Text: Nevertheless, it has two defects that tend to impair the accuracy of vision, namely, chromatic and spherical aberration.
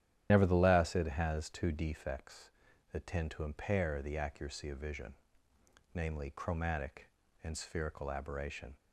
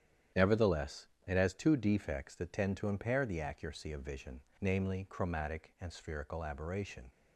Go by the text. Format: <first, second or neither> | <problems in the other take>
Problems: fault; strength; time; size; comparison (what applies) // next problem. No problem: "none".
second | loses the start of "Nevertheless"; at 0.2 s; 50 ms // starts louder than the rest; strong; until 1.3 s; 10.5 dB; strong in the second